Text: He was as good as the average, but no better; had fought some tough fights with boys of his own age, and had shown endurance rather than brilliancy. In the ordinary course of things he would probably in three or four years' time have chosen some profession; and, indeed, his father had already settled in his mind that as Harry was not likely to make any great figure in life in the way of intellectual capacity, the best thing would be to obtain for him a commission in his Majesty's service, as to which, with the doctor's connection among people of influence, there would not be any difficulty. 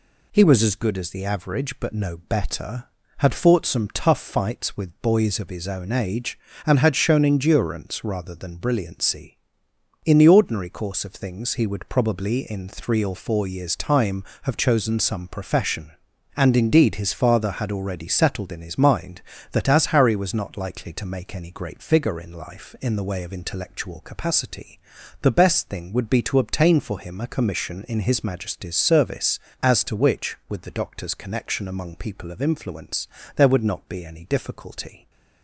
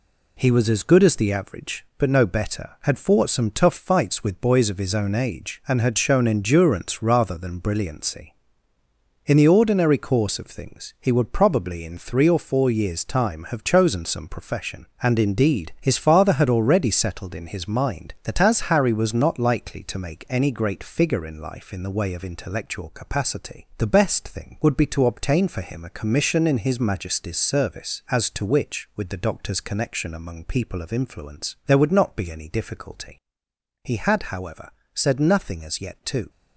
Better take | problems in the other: first | goes on to say "He had however said nothing as yet to"; strong; from 33.8 s on; 2.4 s long

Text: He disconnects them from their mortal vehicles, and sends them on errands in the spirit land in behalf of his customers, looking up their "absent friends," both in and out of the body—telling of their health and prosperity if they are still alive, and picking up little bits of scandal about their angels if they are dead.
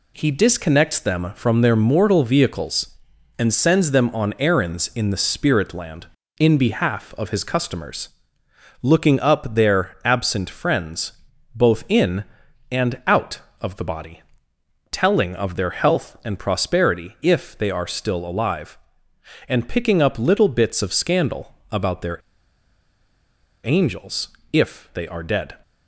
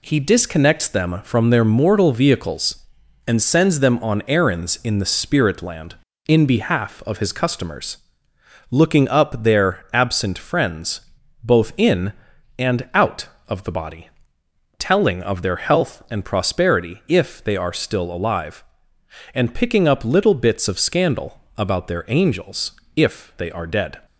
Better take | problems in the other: second | pauses between "scandal" and "about"; slight; at 21.5 s; 0.18 s long; slight in the second // pauses between "their" and "angels"; strong; at 22.1 s; 1.4 s long // pauses between "angels" and "if"; slight; at 24.2 s; 0.24 s long; slight in the second

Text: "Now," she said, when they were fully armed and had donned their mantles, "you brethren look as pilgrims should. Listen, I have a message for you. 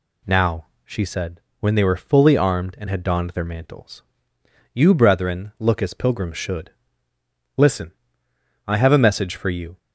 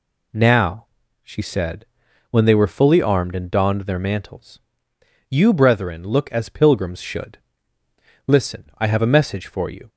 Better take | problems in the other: first | skips "had"; at 3.5 s

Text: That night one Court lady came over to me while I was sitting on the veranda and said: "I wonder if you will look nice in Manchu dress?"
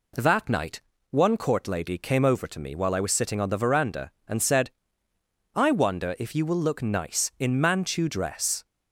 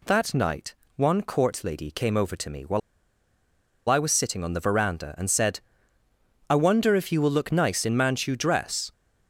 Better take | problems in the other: first | pauses between "night" and "one"; slight; at 0.7 s; 0.22 s long; slight in the first // pauses between "while" and "I"; at 2.8 s; 1.0 s long

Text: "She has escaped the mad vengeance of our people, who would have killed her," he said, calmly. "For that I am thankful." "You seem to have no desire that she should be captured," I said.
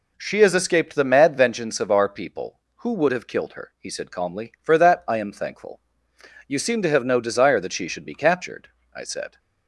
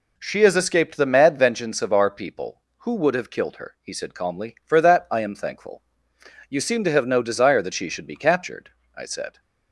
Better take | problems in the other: neither | none

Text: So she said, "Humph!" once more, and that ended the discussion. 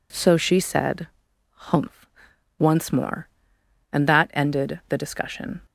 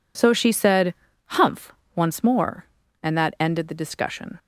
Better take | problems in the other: neither | none

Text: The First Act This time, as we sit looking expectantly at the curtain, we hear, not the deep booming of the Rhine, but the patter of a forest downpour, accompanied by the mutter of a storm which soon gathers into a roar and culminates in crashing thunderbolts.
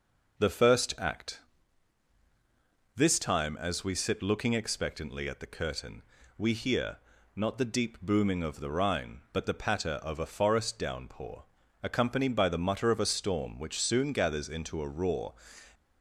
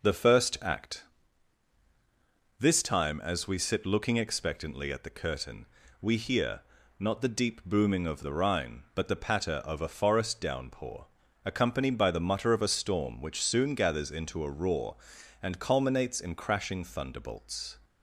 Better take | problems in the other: second | pauses between "Act" and "This"; strong; at 1.3 s; 1.5 s long; strong in the second // stops before "and culminates in crashing thunderbolts"; at 15.7 s

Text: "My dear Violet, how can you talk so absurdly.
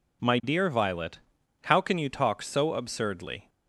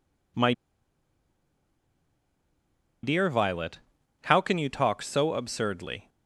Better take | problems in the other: first | pauses between "My" and "dear"; strong; at 0.5 s; 2.5 s long

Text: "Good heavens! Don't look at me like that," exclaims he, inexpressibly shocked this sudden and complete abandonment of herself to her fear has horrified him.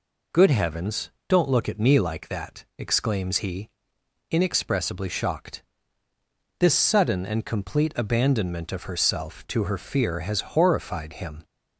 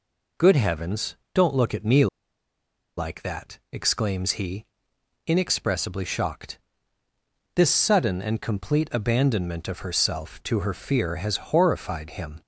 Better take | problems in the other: first | pauses between "me" and "like"; noticeable; at 2.0 s; 0.92 s long // pauses between "shocked" and "this"; noticeable; at 6.5 s; 0.98 s long; noticeable in the first

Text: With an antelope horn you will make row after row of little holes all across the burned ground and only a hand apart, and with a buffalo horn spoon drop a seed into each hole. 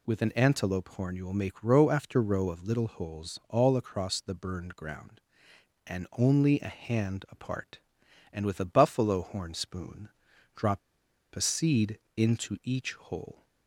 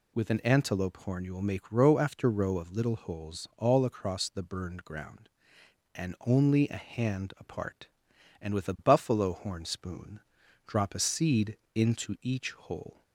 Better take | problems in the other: second | pauses between "spoon" and "drop"; noticeable; at 10.0 s; 0.46 s long; noticeable in the second // pauses between "drop" and "a"; noticeable; at 10.8 s; 0.55 s long // pauses between "seed" and "into"; slight; at 11.9 s; 0.18 s long; slight in the second

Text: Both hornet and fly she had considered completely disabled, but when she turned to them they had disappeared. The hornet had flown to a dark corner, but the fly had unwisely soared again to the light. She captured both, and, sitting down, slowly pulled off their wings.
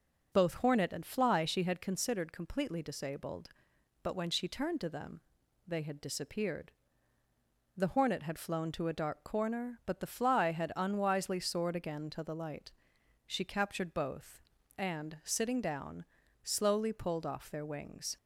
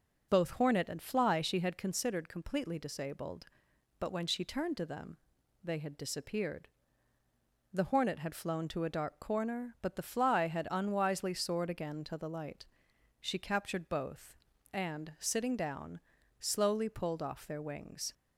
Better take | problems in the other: neither | pauses between "them" and "they"; the same in both

